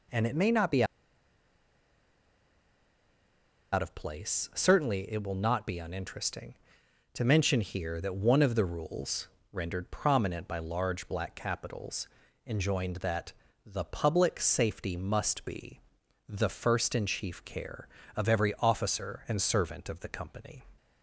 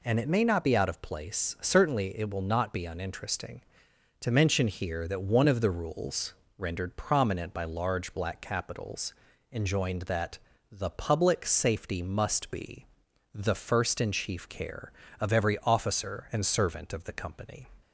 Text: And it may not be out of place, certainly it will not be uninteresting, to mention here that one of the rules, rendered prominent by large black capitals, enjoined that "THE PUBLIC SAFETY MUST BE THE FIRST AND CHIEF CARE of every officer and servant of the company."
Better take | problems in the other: second | pauses between "be" and "out"; strong; at 0.8 s; 2.8 s long // pauses between "that" and "THE"; slight; at 13.3 s; 0.32 s long; slight in the second // pauses between "BE" and "THE"; noticeable; at 15.8 s; 0.48 s long; noticeable in the second

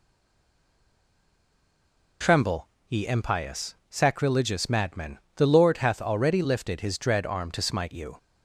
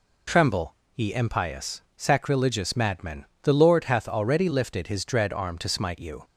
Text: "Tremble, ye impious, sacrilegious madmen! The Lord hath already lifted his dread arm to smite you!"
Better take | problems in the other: second | stays silent before the first word; until 2.2 s; 2.2 s long

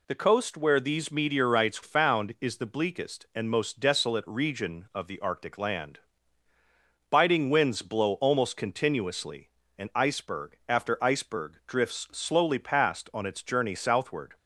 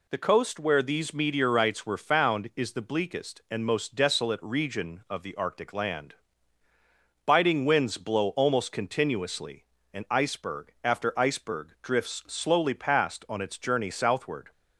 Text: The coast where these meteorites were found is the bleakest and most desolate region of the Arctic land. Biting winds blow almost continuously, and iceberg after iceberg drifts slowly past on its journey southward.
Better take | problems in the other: second | skips "were"; at 1.8 s

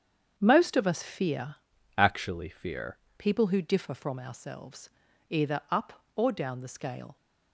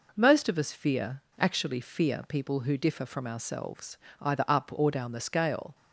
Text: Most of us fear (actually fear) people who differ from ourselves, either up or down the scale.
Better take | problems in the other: second | starts louder than the rest; strong; until 1.3 s; 7.5 dB // changes voice from "actually" to "fear"; from 1.9 to 2.9 s; 1.0 s long

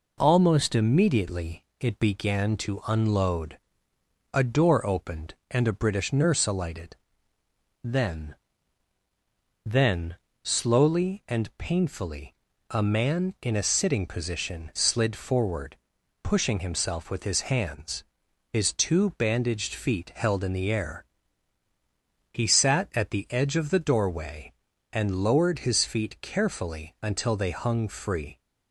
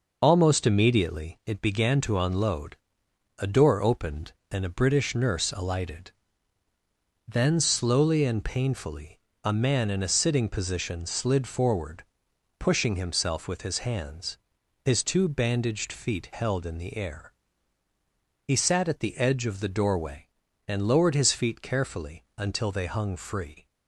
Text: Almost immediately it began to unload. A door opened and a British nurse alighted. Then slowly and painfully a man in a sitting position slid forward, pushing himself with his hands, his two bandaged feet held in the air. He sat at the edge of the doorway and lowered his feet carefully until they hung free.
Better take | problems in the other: second | pauses between "immediately" and "it"; slight; at 1.6 s; 0.16 s long // says "Then" twice; at 9.6 s // pauses between "painfully" and "a"; at 12.3 s; 0.38 s long; slight in the second

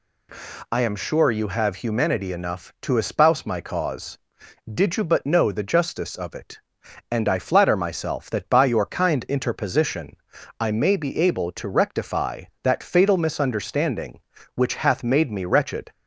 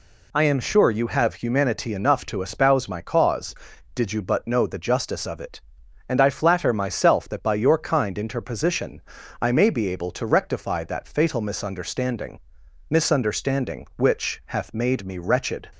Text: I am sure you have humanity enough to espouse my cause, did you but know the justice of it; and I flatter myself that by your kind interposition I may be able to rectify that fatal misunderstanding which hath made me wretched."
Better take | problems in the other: first | pauses between "interposition" and "I"; at 9.0 s; 0.40 s long; also in the first // says "misunderstanding" twice; at 12.9 s

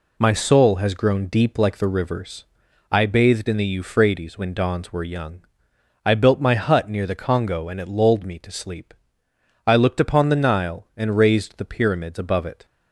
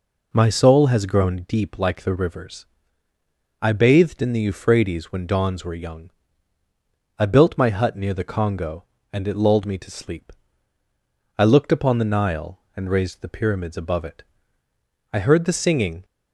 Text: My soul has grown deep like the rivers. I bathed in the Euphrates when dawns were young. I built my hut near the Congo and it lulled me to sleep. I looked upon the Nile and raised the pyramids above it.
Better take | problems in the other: first | goes on to say "I heard the singing"; noticeable; from 15.1 s on; 0.94 s long

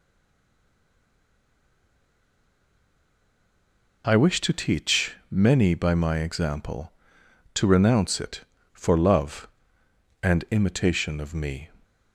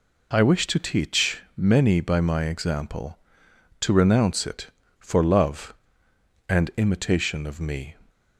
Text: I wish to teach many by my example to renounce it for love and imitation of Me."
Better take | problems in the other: second | stays silent before the first word; strong; until 4.0 s; 4.0 s long // pauses between "teach" and "many"; slight; at 5.1 s; 0.16 s long; slight in the second

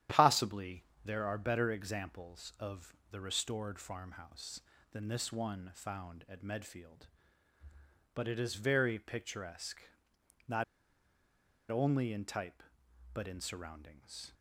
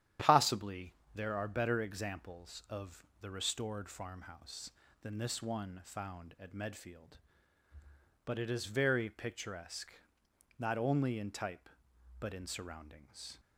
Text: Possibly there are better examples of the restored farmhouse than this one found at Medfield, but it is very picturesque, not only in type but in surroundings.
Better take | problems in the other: second | starts louder than the rest; strong; until 1.3 s; 10.5 dB; strong in the second // pauses between "Possibly" and "there"; slight; at 0.8 s; 0.22 s long; slight in the second // pauses between "of" and "the"; slight; at 2.9 s; 0.16 s long; slight in the second // pauses between "not" and "only"; at 10.6 s; 1.0 s long

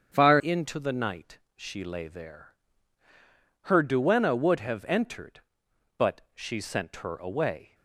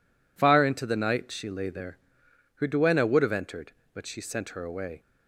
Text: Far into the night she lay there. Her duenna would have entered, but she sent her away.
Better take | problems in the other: second | starts louder than the rest; strong; until 1.1 s; 7.5 dB // changes voice at "into"; from 0.3 s on; 7.4 s long // pauses between "night" and "she"; slight; at 1.3 s; 0.18 s long

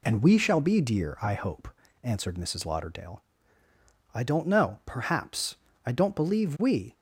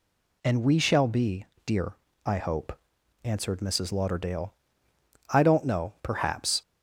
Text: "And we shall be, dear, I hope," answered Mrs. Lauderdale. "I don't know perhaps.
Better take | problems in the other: second | goes on to say "I don't believe we"; noticeable; from 5.8 s on; 1.0 s long

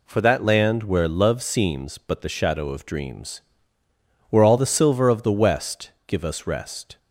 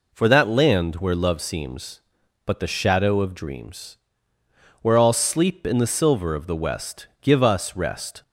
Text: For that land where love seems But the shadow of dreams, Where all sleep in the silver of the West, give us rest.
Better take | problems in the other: second | skips "sleep in"; at 4.5 s

